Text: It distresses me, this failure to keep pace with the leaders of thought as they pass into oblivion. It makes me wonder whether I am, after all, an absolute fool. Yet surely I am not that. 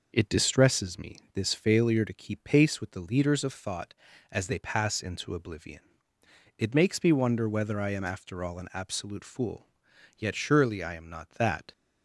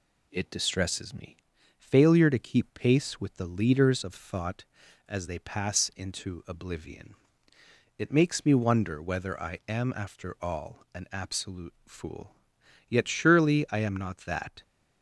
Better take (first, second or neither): first